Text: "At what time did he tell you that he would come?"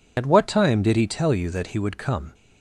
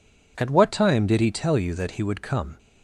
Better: second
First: loses the start of "At"; at 0.1 s; 65 ms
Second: none

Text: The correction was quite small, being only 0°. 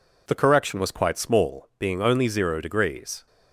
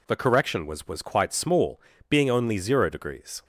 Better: first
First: none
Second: says "was" twice; at 0.8 s

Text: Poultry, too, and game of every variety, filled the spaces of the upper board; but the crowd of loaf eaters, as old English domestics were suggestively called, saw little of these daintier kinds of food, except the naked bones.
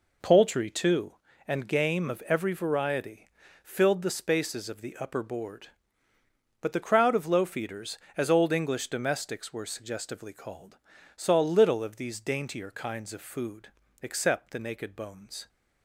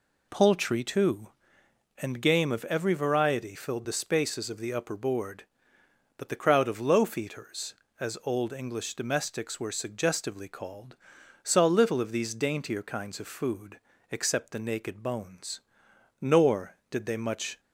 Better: first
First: none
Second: goes on to say "Nor did they much"; from 16.2 s on; 1.3 s long

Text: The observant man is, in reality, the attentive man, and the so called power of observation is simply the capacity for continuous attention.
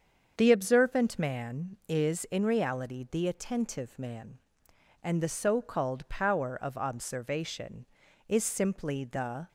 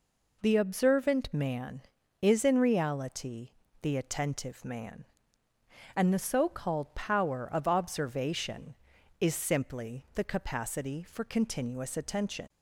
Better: second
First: starts louder than the rest; strong; until 1.3 s; 7 dB // stops before "capacity for continuous attention"; at 9.4 s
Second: none

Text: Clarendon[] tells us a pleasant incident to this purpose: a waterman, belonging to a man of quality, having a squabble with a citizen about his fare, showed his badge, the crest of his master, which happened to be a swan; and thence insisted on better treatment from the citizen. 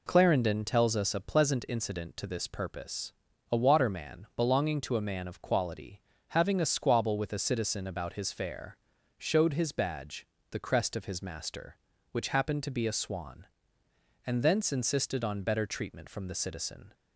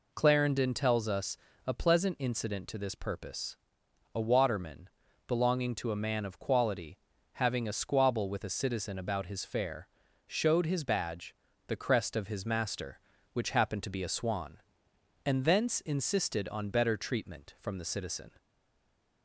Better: first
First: none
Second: pauses between "us" and "a"; slight; at 1.3 s; 0.30 s long // stays silent after the last word; slight; from 18.3 s on; 0.9 s long

